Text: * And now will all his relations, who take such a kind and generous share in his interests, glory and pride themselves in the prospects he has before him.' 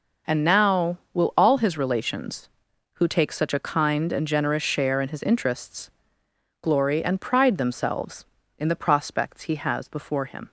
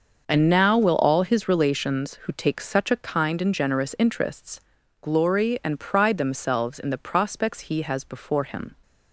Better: first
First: none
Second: starts louder than the rest; until 1.2 s; 6 dB // skips "share in his"; at 3.9 s

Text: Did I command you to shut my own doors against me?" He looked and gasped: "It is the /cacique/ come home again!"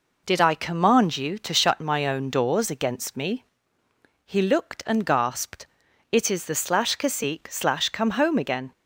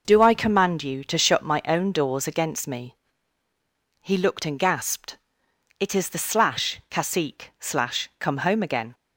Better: first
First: none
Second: says "Do" for "Did"; at 0.0 s

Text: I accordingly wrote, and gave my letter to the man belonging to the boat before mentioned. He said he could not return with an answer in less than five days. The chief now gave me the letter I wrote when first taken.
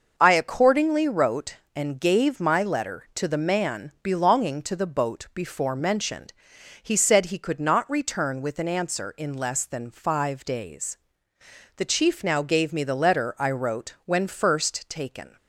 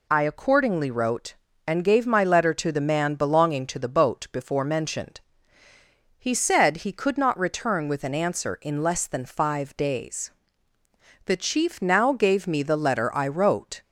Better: first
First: none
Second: stops before "when first taken"; at 13.8 s

